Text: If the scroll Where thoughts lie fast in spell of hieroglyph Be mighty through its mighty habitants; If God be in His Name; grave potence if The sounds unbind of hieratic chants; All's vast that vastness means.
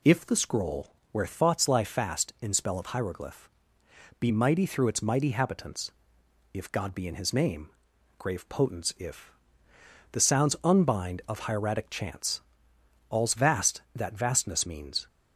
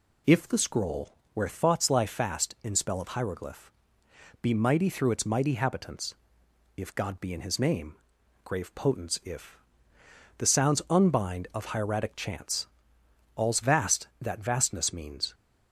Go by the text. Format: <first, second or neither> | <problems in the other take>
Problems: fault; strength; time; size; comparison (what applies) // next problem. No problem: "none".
neither | pauses between "scroll" and "Where"; slight; the same in both // pauses between "hieroglyph" and "Be"; noticeable; the same in both // pauses between "if" and "The"; noticeable; the same in both